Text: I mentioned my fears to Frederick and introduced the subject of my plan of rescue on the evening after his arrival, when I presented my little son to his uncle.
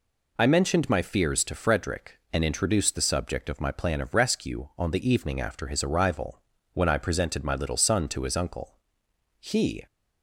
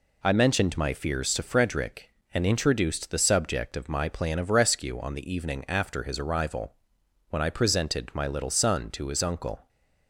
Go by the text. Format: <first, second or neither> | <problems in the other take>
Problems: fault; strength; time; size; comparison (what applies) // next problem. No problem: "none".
second | goes on to say "He"; slight; from 9.3 s on; 0.46 s long